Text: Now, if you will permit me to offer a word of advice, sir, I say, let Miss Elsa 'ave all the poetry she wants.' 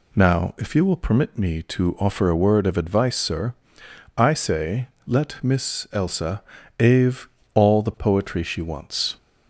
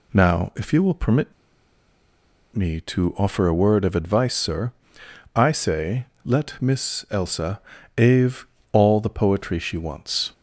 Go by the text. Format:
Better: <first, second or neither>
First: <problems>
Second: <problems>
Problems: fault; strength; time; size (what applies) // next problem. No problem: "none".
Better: first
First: pauses between "Elsa" and "ave"; slight; at 6.4 s; 0.36 s long // pauses between "ave" and "all"; slight; at 7.2 s; 0.30 s long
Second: pauses between "permit" and "me"; at 1.3 s; 1.2 s long // pauses between "Elsa" and "ave"; slight; at 7.6 s; 0.36 s long // pauses between "ave" and "all"; slight; at 8.4 s; 0.30 s long